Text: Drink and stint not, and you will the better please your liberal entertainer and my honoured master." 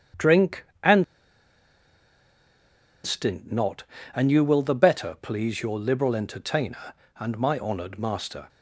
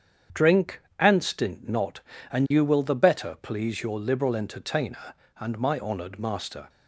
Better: second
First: starts louder than the rest; strong; until 3.3 s; 8 dB // pauses between "and" and "stint"; strong; at 1.0 s; 1.9 s long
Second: starts louder than the rest; strong; until 1.5 s; 8 dB

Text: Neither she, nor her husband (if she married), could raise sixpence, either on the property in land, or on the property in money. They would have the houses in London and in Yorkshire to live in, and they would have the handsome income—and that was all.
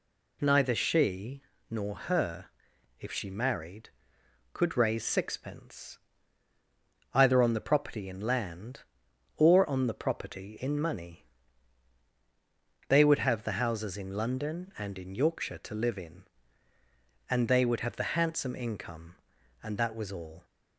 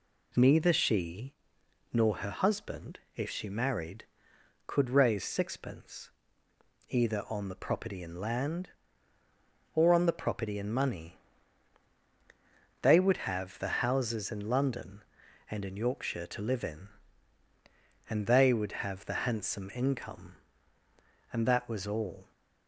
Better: second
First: skips "husband"; at 2.7 s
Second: none

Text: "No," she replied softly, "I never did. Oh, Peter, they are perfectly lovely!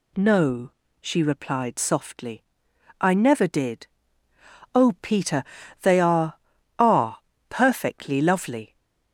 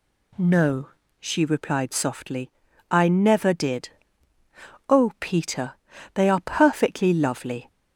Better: second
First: says "are" twice; at 6.7 s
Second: none

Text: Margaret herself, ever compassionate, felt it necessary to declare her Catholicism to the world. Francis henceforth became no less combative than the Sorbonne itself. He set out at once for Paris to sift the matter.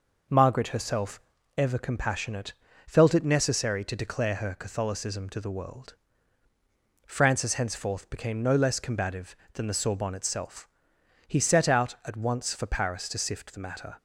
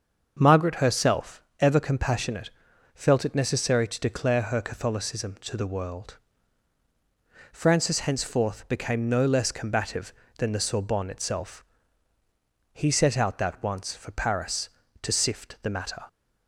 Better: first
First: none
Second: starts louder than the rest; until 1.4 s; 7 dB // says "that" for "at"; at 13.3 s

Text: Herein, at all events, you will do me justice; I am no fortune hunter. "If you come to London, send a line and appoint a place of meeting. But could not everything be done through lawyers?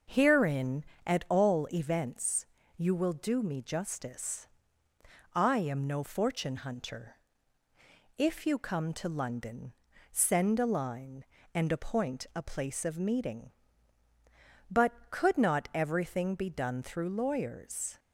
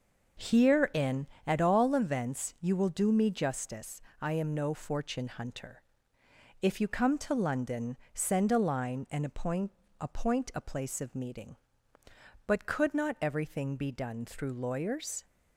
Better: first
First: starts louder than the rest; noticeable; until 1.3 s; 6 dB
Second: starts louder than the rest; noticeable; until 1.6 s; 6 dB // says "appoint" twice; at 10.0 s

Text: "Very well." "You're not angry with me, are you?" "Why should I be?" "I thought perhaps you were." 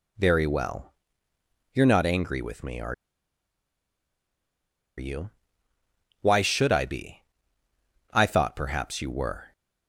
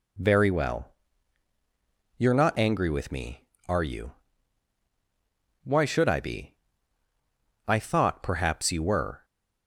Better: second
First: pauses between "are" and "you"; strong; at 2.9 s; 2.0 s long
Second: none

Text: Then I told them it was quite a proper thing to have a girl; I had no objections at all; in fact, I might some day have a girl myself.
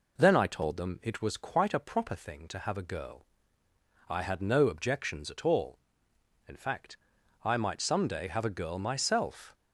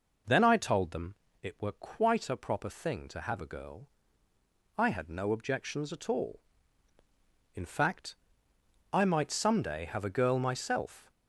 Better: first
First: none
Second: pauses between "them" and "it"; slight; at 1.1 s; 0.26 s long // says "were" for "was"; at 1.6 s

